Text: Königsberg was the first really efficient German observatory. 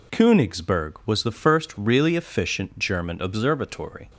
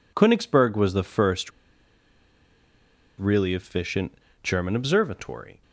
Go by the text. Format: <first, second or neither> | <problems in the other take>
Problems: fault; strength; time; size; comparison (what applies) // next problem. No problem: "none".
first | pauses between "first" and "really"; strong; at 1.5 s; 1.6 s long // pauses between "efficient" and "German"; slight; at 4.1 s; 0.30 s long